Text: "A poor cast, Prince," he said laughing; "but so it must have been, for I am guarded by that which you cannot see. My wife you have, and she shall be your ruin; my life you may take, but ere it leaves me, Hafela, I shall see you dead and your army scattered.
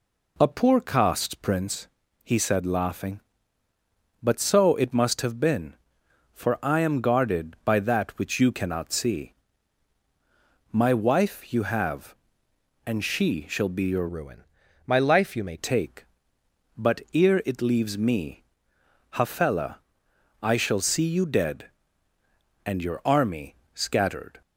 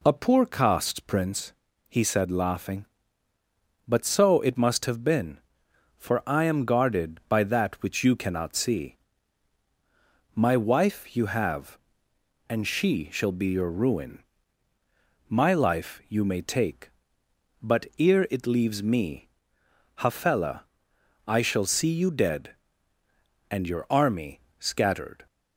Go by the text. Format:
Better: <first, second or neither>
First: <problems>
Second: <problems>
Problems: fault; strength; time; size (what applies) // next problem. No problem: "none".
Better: second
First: changes voice from "ruin" to "may"; from 14.0 to 15.5 s; 1.5 s long // pauses between "army" and "scattered"; slight; at 23.5 s; 0.18 s long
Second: pauses between "army" and "scattered"; slight; at 24.4 s; 0.18 s long